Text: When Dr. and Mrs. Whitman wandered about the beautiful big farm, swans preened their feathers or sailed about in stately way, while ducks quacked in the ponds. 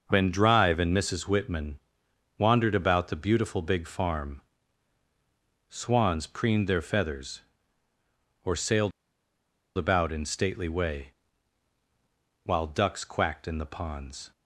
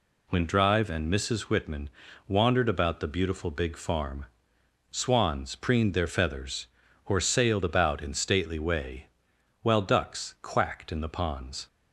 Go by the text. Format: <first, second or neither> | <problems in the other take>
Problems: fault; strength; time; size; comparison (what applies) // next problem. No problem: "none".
second | pauses between "Whitman" and "wandered"; noticeable; at 1.7 s; 0.60 s long; also in the second // pauses between "sailed" and "about"; noticeable; at 8.9 s; 0.86 s long